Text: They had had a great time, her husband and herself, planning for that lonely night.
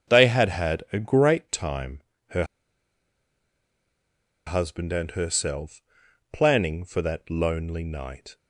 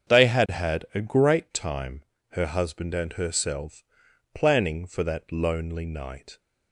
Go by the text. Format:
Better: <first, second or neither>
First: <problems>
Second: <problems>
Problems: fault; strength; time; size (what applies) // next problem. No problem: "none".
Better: second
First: starts louder than the rest; strong; until 1.1 s; 7.5 dB // pauses between "her" and "husband"; strong; at 2.4 s; 2.0 s long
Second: starts louder than the rest; strong; until 1.1 s; 7.5 dB